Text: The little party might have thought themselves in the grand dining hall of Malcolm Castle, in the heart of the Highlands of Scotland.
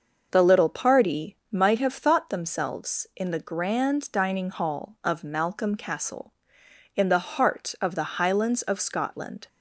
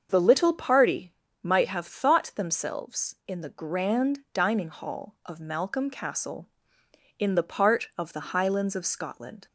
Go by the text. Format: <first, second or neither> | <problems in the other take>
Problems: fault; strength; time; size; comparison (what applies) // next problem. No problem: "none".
first | starts louder than the rest; until 1.1 s; 6.5 dB; noticeable in the first // pauses between "party" and "might"; slight; at 1.1 s; 0.28 s long // says "part" for "heart"; at 7.4 s